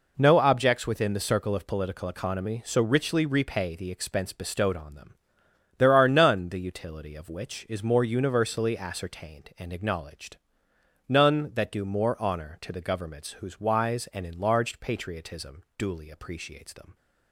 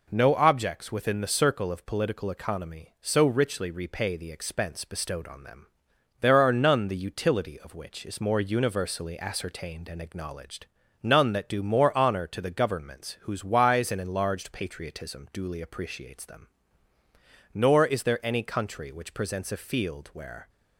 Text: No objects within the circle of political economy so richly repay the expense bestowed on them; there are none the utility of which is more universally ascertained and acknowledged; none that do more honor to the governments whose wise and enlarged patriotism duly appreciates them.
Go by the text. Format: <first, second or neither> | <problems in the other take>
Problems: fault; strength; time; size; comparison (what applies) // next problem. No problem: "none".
first | goes on to say "Nor is there any country which presents a field where"; strong; from 17.5 s on; 2.9 s long